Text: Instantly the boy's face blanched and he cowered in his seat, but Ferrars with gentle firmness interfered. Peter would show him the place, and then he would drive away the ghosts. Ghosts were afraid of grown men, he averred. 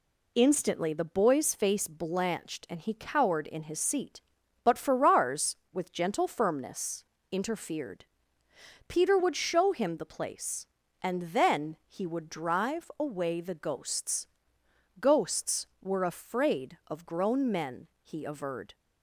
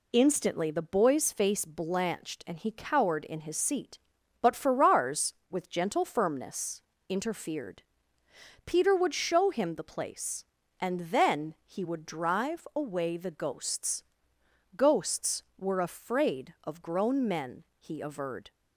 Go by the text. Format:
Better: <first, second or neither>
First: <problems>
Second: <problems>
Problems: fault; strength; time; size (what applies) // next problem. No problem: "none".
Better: neither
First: pauses between "firmness" and "interfered"; slight; at 7.0 s; 0.28 s long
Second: pauses between "firmness" and "interfered"; slight; at 6.8 s; 0.28 s long